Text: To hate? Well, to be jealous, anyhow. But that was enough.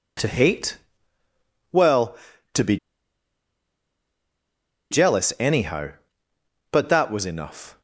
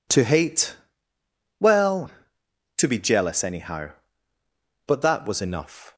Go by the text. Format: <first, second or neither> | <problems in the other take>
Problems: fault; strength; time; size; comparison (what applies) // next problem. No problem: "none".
second | pauses between "be" and "jealous"; strong; at 2.7 s; 2.1 s long